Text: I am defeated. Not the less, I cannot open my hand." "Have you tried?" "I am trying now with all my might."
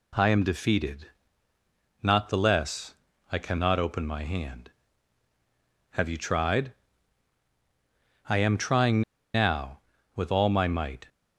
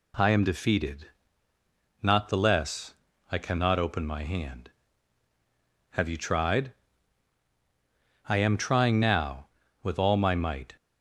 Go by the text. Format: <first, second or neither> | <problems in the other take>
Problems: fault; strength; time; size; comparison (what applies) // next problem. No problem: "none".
second | pauses between "trying" and "now"; slight; at 9.0 s; 0.32 s long